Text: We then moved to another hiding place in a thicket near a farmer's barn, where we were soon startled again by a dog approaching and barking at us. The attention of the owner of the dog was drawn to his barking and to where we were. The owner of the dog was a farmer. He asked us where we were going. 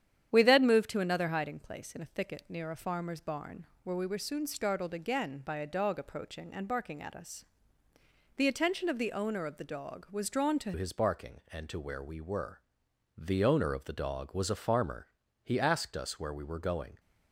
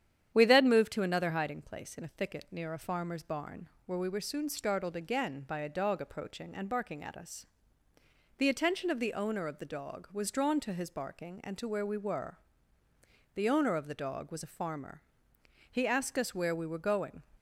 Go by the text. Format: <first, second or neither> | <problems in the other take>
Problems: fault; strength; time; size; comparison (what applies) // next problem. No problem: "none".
second | starts louder than the rest; strong; until 1.3 s; 9.5 dB; strong in the second // changes voice at "his"; from 10.7 s on; 6.2 s long